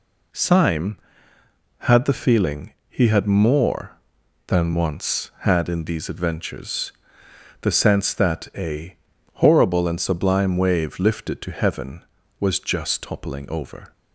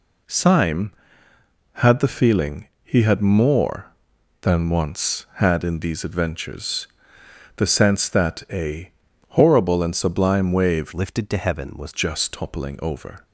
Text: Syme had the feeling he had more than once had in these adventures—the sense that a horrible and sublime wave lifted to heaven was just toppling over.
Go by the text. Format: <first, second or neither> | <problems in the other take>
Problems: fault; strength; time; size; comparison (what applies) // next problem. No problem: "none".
first | pauses between "feeling" and "he"; slight; at 2.6 s; 0.16 s long; slight in the first // pauses between "a" and "horrible"; at 8.9 s; 0.38 s long; also in the first // changes voice from "lifted" to "was"; from 10.9 to 11.9 s; 1.0 s long